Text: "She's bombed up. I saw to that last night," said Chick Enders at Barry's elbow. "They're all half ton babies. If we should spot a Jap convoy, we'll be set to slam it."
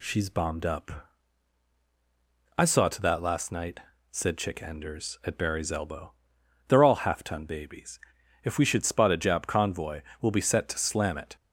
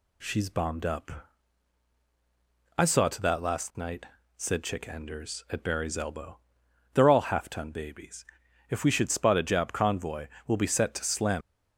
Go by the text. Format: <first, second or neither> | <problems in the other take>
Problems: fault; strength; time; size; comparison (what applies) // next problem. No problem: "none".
first | stops before "it"; at 11.4 s